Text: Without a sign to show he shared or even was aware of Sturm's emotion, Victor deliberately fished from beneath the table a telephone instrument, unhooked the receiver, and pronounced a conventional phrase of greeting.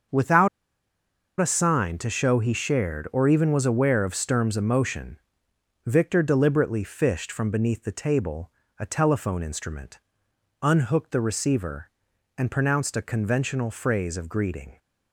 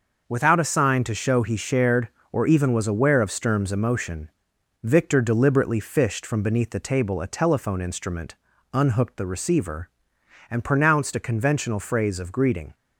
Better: second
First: starts louder than the rest; until 2.0 s; 6.5 dB // pauses between "Without" and "a"; noticeable; at 0.4 s; 0.91 s long // pauses between "table" and "a"; slight; at 8.5 s; 0.30 s long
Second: none

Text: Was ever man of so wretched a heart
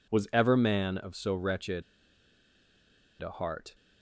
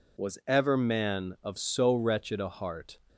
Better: second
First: pauses between "wretched" and "a"; strong; at 1.8 s; 1.3 s long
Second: none

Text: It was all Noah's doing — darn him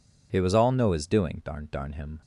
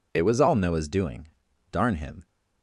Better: second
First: says "darn" twice; at 1.7 s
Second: none

